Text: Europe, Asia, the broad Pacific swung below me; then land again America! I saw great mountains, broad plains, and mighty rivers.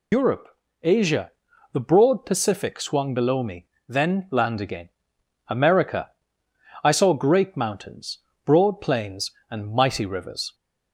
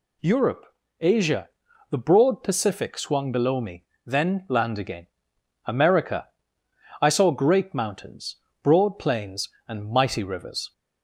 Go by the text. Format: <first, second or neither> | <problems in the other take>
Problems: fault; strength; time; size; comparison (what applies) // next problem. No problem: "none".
second | loses the start of "Europe"; at 0.1 s; 95 ms // pauses between "again" and "America"; noticeable; at 4.8 s; 0.58 s long; noticeable in the second